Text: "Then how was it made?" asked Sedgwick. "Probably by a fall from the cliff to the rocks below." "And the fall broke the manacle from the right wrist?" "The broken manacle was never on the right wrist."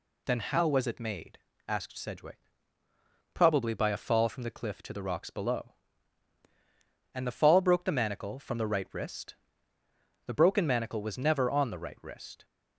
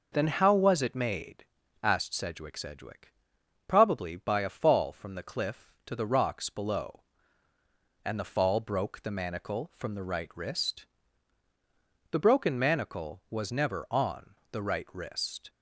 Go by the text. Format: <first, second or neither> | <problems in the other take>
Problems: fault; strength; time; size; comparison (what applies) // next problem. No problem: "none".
first | says "Sedgwick" twice; at 2.5 s // pauses between "on" and "the"; slight; at 14.3 s; 0.16 s long